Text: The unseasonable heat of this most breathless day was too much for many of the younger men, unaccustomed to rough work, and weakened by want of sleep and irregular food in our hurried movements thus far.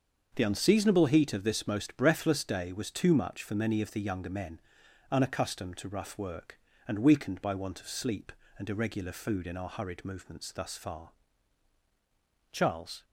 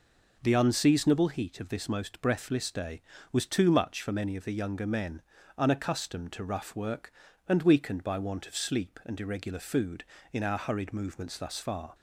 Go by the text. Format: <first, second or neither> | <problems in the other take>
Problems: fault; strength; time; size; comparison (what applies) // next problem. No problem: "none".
second | starts louder than the rest; until 1.3 s; 6.5 dB // goes on to say "Charles"; from 12.5 s on; 0.54 s long